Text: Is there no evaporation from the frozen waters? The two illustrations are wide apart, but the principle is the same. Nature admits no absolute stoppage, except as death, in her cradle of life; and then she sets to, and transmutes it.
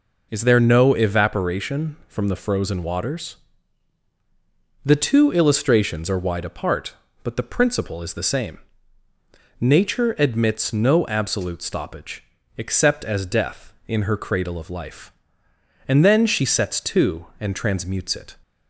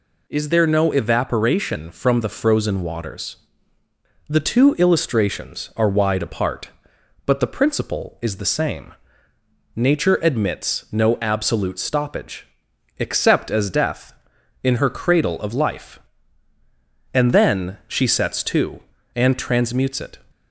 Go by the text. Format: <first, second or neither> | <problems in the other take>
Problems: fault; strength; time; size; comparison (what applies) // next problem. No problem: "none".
neither | none